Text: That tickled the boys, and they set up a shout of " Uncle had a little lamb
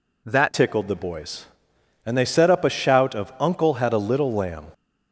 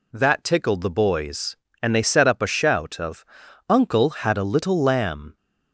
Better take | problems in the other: second | changes voice at "tickled"; from 0.5 s on; 4.2 s long

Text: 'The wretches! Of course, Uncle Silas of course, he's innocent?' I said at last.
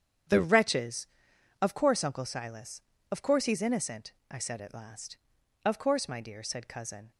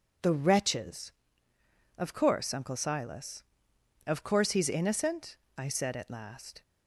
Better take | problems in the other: second | starts louder than the rest; strong; until 1.8 s; 8.5 dB // goes on to say "Of course my dear said Cousin"; from 5.6 s on; 1.4 s long

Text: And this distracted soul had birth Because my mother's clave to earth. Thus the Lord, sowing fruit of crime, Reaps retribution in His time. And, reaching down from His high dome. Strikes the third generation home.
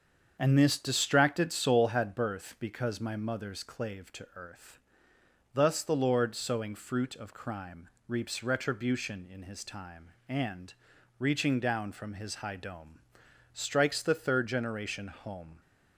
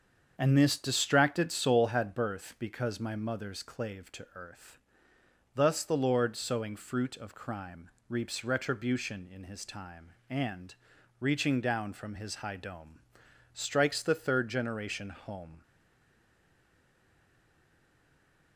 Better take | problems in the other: first | starts louder than the rest; strong; until 1.3 s; 7 dB; strong in the first // stays silent after the last word; strong; from 15.6 s on; 2.9 s long

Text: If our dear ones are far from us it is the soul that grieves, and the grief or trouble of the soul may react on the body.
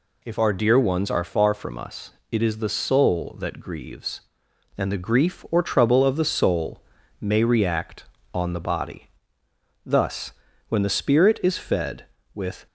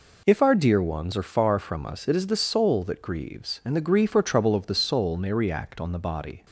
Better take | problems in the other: second | pauses between "us" and "it"; slight; at 2.1 s; 0.18 s long // pauses between "soul" and "may"; at 6.7 s; 0.40 s long // goes on to say "Thus when the Spirit is fed with"; strong; from 9.8 s on; 2.8 s long

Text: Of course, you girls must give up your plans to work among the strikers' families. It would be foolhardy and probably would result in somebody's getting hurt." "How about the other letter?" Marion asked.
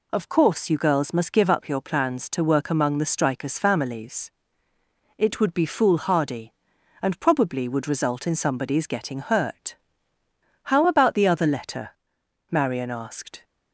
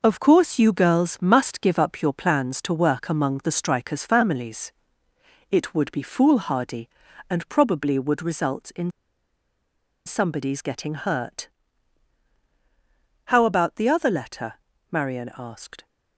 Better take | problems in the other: first | pauses between "in" and "somebody's"; at 8.8 s; 1.1 s long

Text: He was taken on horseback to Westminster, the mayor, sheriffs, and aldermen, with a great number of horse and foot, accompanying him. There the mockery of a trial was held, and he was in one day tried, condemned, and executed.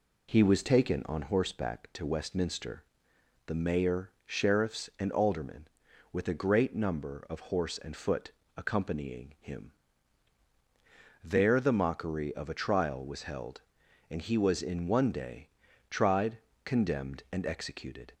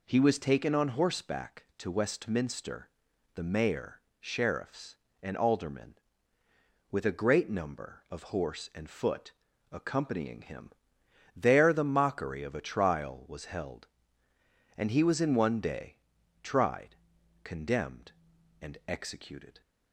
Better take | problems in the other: neither | pauses between "day" and "tried"; the same in both

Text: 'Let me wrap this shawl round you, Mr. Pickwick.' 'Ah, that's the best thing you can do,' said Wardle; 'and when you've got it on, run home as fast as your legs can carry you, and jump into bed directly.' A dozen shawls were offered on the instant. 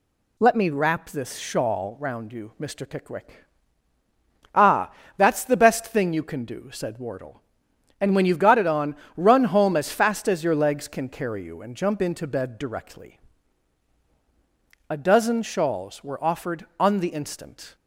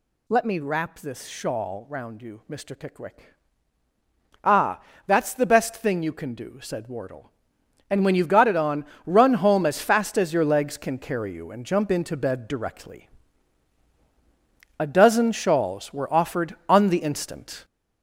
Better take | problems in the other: first | gets louder; noticeable; throughout; 6 dB

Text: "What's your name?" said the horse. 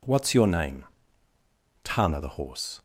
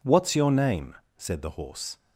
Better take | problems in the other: second | says "tana" for "said"; at 1.8 s

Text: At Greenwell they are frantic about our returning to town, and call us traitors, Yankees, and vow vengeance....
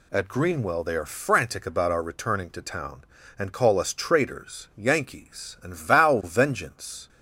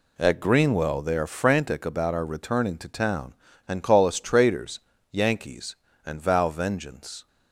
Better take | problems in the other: neither | none

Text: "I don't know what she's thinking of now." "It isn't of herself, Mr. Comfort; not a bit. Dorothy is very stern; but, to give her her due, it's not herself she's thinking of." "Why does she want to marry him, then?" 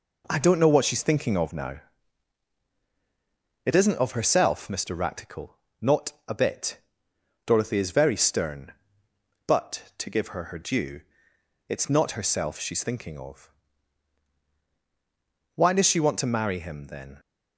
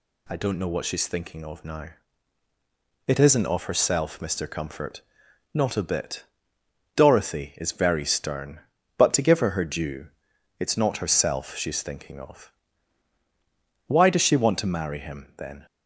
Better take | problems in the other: second | says "Ractical" for "Comfort"; at 4.9 s

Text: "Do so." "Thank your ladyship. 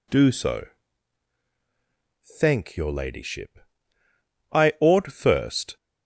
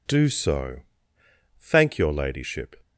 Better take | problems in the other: second | goes on to say "I ought first"; noticeable; from 4.5 s on; 1.2 s long

